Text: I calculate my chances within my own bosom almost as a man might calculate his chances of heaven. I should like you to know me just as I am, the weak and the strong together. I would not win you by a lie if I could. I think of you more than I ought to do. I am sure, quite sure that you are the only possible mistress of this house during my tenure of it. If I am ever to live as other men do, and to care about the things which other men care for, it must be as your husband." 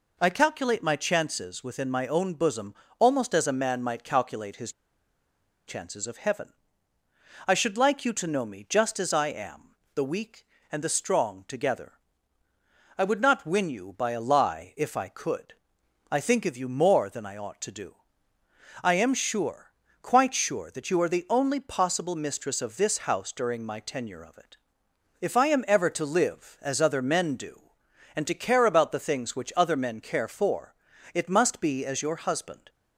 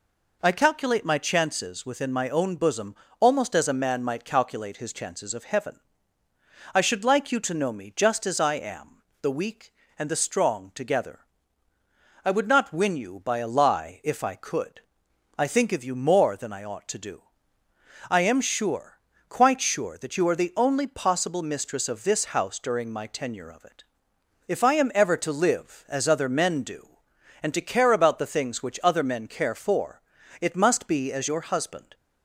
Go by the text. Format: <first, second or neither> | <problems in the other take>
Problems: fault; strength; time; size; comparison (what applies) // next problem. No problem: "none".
second | pauses between "bosom" and "almost"; slight; at 2.7 s; 0.26 s long; slight in the second // pauses between "his" and "chances"; noticeable; at 4.7 s; 0.95 s long